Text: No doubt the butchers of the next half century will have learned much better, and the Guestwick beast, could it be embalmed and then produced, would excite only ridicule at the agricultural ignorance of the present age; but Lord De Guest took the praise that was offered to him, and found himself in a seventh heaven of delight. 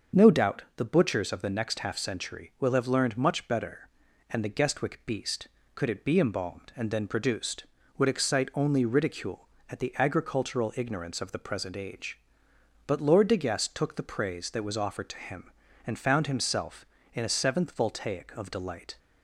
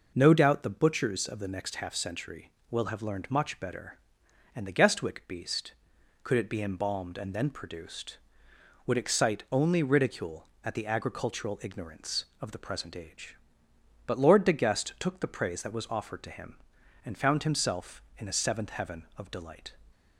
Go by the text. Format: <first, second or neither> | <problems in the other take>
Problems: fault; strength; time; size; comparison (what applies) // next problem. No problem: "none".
second | starts louder than the rest; until 1.3 s; 6.5 dB // says "voltaic" for "heaven"; at 17.7 s